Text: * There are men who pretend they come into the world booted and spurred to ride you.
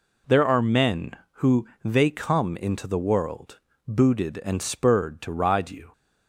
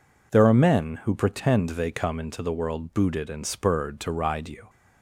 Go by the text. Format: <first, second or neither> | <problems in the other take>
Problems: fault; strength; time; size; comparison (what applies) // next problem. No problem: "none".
second | skips "pretend"; at 1.7 s // pauses between "world" and "booted"; slight; at 3.6 s; 0.26 s long